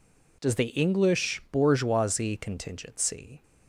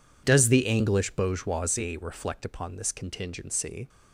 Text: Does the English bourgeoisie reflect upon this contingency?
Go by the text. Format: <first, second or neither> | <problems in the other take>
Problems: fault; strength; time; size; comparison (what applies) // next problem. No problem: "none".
second | skips "reflect upon this"; at 2.3 s